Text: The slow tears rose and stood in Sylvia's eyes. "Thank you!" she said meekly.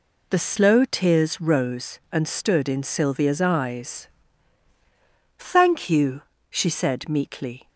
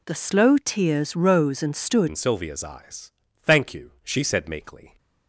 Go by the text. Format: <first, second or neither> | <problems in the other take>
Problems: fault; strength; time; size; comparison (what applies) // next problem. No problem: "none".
first | changes voice at "in"; from 2.0 s on; 2.9 s long